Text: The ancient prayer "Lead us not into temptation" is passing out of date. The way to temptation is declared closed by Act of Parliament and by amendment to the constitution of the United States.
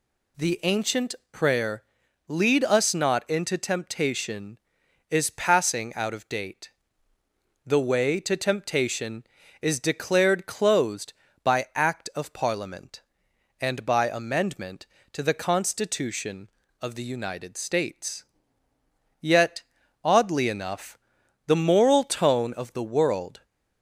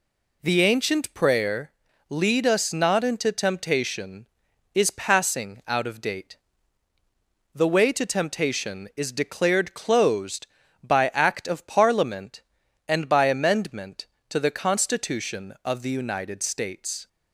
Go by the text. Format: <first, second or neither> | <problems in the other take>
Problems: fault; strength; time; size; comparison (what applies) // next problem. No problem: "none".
second | pauses between "ancient" and "prayer"; slight; at 1.1 s; 0.16 s long // pauses between "prayer" and "Lead"; at 1.8 s; 0.42 s long; also in the second // goes on to say "Yet oddly enough the moral tone of the world"; strong; from 19.2 s on; 4.2 s long